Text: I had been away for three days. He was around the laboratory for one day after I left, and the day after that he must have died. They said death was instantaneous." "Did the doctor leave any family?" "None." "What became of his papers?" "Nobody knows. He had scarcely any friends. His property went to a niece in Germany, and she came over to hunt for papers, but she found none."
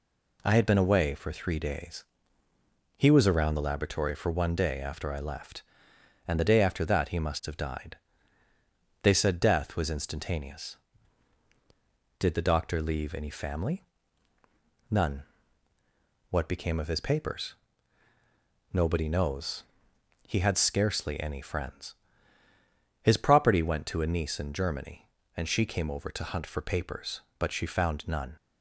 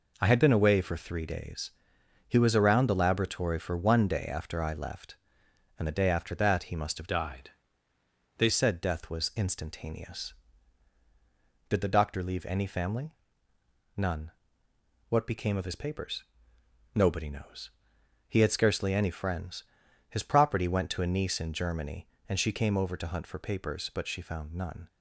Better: first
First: none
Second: changes voice from "died" to "They"; from 7.0 to 8.4 s; 1.4 s long

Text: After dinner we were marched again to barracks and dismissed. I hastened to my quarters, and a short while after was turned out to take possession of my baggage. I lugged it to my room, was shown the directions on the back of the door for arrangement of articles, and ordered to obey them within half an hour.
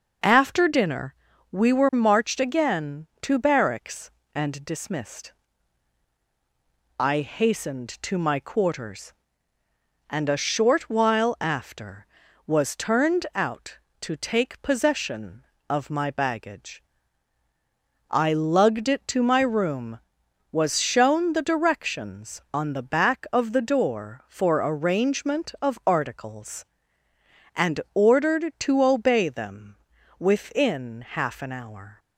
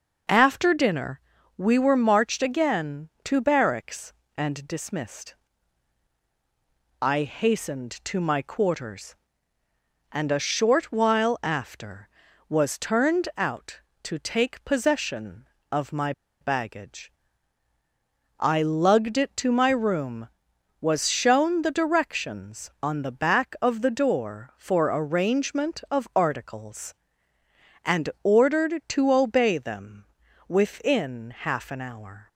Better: first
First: pauses between "dinner" and "we"; slight; at 1.1 s; 0.36 s long // pauses between "them" and "within"; at 29.7 s; 0.42 s long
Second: pauses between "dinner" and "we"; slight; at 1.2 s; 0.36 s long // pauses between "my" and "baggage"; slight; at 16.1 s; 0.29 s long // pauses between "them" and "within"; at 30.0 s; 0.42 s long

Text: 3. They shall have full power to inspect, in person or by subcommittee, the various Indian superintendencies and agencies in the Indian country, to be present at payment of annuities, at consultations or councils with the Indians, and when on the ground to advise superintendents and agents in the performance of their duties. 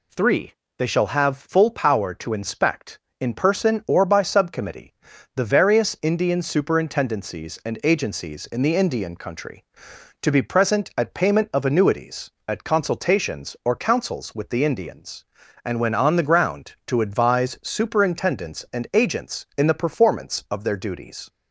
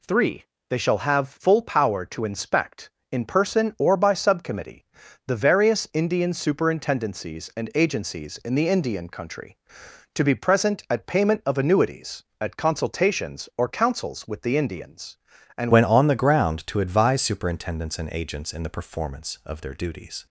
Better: first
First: none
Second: changes voice at "when"; from 15.7 s on; 4.5 s long

